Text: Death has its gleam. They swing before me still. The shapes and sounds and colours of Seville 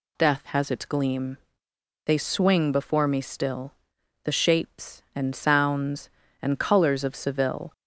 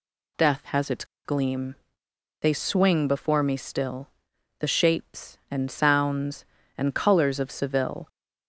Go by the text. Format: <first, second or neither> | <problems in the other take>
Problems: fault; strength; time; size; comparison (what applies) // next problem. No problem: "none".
first | pauses between "its" and "gleam"; slight; at 1.0 s; 0.20 s long